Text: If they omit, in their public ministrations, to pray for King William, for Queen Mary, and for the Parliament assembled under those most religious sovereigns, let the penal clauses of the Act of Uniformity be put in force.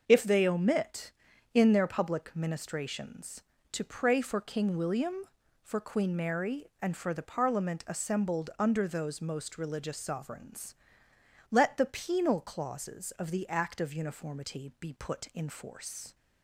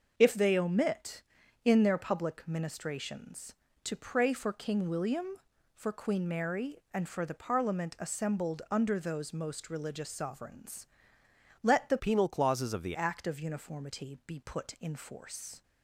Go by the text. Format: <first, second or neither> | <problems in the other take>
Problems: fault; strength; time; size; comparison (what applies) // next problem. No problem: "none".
first | starts louder than the rest; until 1.1 s; 6 dB; also in the first // changes voice from "penal" to "the"; from 11.9 to 12.9 s; 1.0 s long